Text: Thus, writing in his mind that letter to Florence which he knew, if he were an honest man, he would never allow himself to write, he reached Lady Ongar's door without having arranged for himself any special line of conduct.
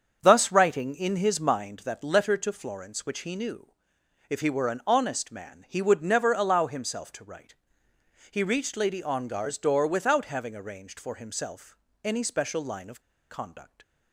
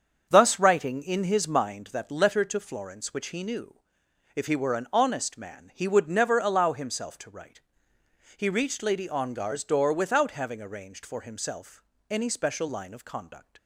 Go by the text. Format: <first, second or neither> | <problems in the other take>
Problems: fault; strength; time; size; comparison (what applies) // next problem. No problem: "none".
second | starts louder than the rest; until 1.2 s; 7 dB; also in the second // pauses between "himself" and "any"; slight; at 11.7 s; 0.28 s long; slight in the second // pauses between "of" and "conduct"; slight; at 12.9 s; 0.30 s long